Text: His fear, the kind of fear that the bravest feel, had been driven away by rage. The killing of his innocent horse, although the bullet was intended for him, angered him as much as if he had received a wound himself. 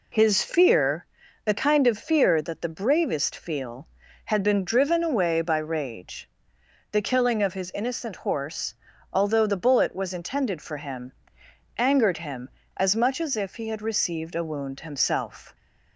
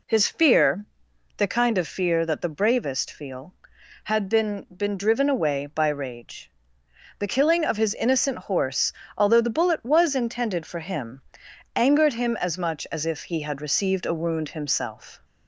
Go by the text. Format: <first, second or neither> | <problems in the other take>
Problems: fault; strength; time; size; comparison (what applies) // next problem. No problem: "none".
first | says "been" twice; at 4.6 s